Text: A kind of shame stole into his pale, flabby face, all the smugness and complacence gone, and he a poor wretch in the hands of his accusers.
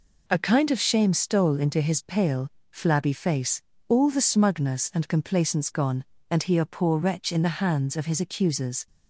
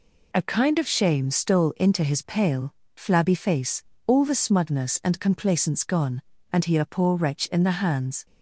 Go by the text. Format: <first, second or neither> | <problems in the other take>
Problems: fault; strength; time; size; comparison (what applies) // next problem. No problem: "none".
first | stops before "of his accusers"; at 8.2 s